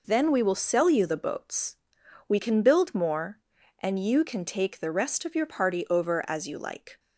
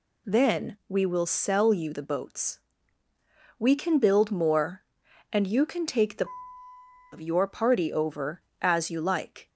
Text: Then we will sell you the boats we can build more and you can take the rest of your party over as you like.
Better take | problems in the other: first | pauses between "boats" and "we"; at 2.5 s; 1.0 s long; noticeable in the first // skips "rest"; at 6.6 s

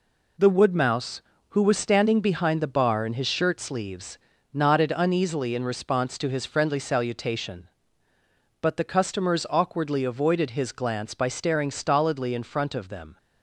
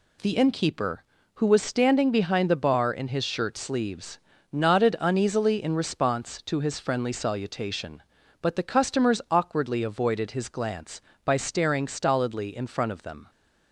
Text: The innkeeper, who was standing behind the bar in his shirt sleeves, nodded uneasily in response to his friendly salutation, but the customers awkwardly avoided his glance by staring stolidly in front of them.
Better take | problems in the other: second | says "woodmouse" for "innkeeper"; at 0.5 s

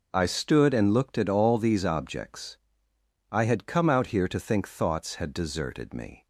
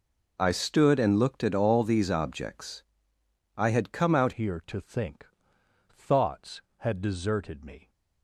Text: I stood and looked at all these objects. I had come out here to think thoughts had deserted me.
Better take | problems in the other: first | changes voice at "here"; from 4.3 s on; 3.5 s long // pauses between "think" and "thoughts"; noticeable; at 5.2 s; 0.68 s long

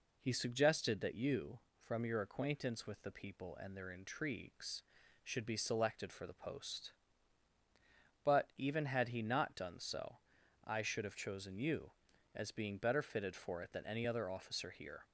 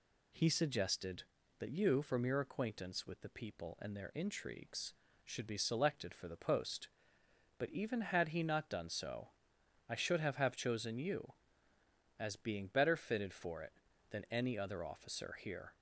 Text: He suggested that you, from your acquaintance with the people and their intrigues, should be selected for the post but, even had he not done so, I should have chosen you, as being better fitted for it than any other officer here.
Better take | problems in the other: first | says "have" twice; at 10.3 s

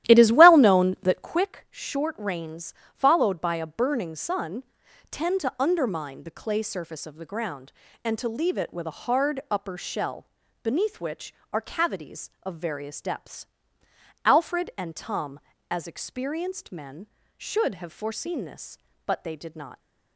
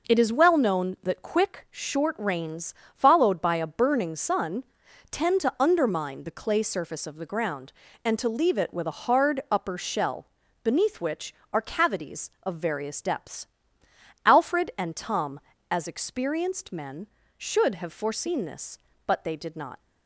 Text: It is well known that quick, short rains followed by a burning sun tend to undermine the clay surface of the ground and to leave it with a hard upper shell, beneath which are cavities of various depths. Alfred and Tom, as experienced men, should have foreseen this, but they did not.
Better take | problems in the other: second | starts louder than the rest; strong; until 1.4 s; 13.5 dB // pauses between "rains" and "followed"; slight; at 2.7 s; 0.20 s long; slight in the second // pauses between "sun" and "tend"; noticeable; at 4.6 s; 0.48 s long; noticeable in the second

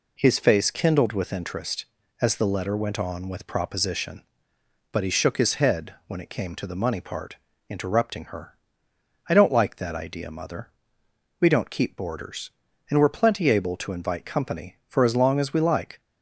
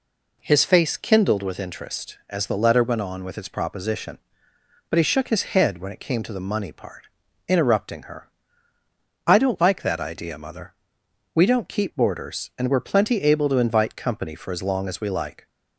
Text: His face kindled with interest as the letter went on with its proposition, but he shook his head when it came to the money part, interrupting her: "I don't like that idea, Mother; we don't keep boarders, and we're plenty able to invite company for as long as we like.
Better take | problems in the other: second | skips "its"; at 3.4 s

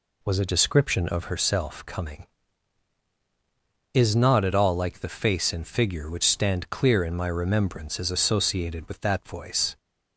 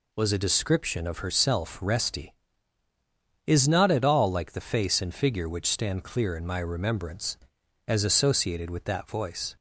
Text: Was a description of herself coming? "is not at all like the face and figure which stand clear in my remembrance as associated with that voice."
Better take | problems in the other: first | says "resty" for "coming"; at 1.8 s

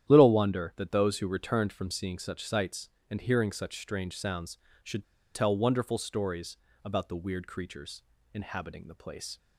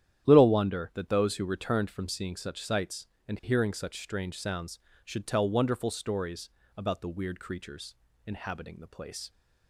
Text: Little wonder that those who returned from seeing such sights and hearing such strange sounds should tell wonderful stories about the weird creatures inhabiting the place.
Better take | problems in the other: second | starts louder than the rest; strong; until 1.1 s; 10.5 dB; strong in the second // pauses between "should" and "tell"; slight; at 5.0 s; 0.28 s long // pauses between "stories" and "about"; slight; at 6.5 s; 0.26 s long; slight in the second // pauses between "creatures" and "inhabiting"; slight; at 8.0 s; 0.32 s long; slight in the second

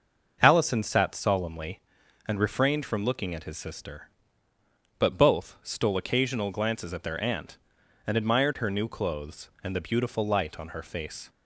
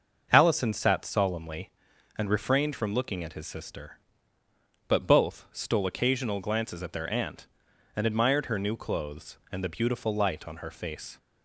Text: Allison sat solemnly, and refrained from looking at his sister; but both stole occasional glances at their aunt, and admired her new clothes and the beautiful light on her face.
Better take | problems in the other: neither | starts louder than the rest; the same in both

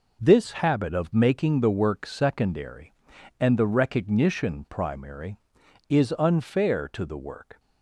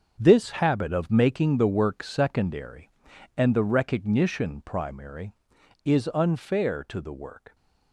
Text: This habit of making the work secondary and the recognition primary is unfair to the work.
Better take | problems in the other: first | gets quieter; strong; throughout; 11 dB

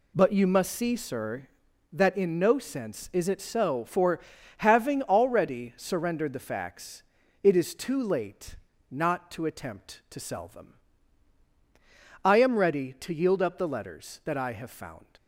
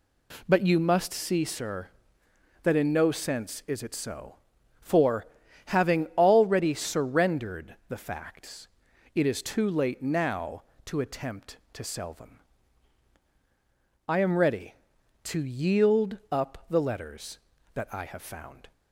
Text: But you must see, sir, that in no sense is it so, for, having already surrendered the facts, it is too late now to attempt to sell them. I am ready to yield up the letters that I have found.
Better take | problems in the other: second | says "not" for "now"; at 8.9 s

